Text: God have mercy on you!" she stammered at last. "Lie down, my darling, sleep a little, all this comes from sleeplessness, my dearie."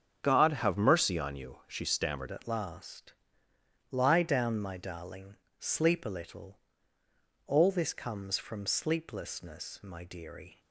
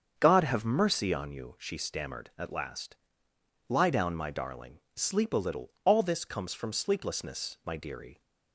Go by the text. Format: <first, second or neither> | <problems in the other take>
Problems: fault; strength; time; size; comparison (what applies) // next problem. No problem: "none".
second | starts louder than the rest; strong; until 1.2 s; 8 dB; strong in the second // changes voice at "at"; from 2.3 s on; 8.2 s long